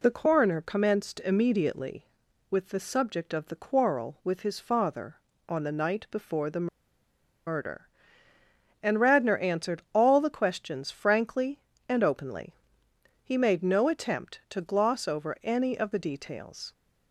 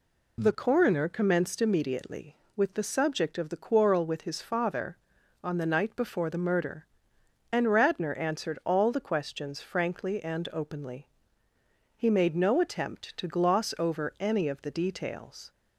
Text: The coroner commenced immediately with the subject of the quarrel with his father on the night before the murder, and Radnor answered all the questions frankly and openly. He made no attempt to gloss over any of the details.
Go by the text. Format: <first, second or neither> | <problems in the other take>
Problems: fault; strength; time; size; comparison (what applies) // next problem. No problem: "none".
second | pauses between "the" and "murder"; noticeable; at 6.6 s; 0.80 s long